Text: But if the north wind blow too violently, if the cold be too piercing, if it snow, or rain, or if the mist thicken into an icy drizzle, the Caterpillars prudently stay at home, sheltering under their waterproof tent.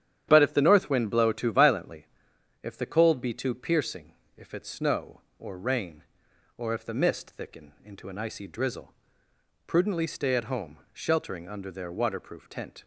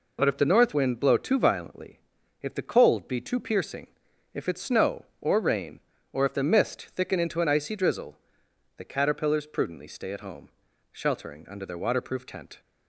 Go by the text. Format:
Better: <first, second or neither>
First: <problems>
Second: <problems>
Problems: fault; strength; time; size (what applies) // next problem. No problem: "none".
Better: second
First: starts louder than the rest; strong; until 1.3 s; 10 dB // skips "the Caterpillars"; at 9.2 s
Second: none